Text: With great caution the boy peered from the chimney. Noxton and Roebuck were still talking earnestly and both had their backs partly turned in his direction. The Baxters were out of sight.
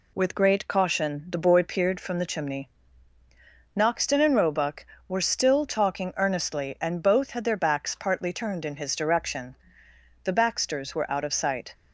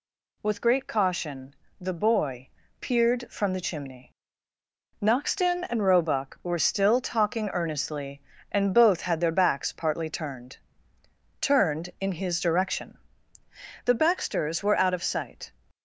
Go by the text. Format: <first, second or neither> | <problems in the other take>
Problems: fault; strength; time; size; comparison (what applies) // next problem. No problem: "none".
first | pauses between "caution" and "the"; slight; at 1.5 s; 0.24 s long // pauses between "boy" and "peered"; slight; at 2.4 s; 0.30 s long // says "turned" twice; at 11.3 s